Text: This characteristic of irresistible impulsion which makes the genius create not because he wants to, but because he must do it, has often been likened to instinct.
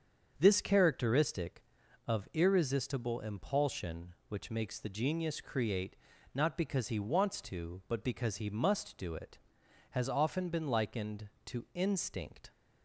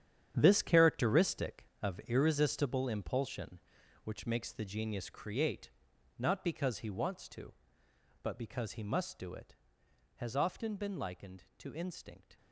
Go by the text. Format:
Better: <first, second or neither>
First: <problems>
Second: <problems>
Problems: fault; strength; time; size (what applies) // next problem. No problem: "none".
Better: first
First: starts louder than the rest; until 1.3 s; 7 dB // pauses between "create" and "not"; at 5.9 s; 0.38 s long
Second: gets quieter; strong; throughout; 11.5 dB // starts louder than the rest; strong; until 1.3 s; 9.5 dB // pauses between "create" and "not"; noticeable; at 5.6 s; 0.48 s long